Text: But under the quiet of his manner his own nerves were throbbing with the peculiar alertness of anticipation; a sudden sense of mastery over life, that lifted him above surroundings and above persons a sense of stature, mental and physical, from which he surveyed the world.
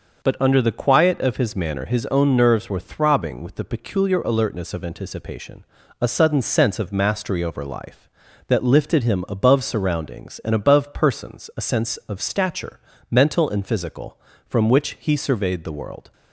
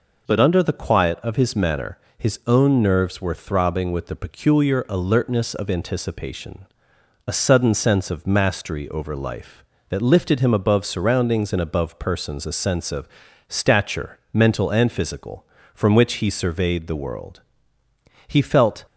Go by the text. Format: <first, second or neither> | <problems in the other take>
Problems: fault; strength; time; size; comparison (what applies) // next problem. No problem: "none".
first | pauses between "manner" and "his"; slight; at 1.9 s; 0.20 s long // pauses between "of" and "stature"; at 13.0 s; 0.40 s long // goes on to say "He felt"; from 18.2 s on; 0.58 s long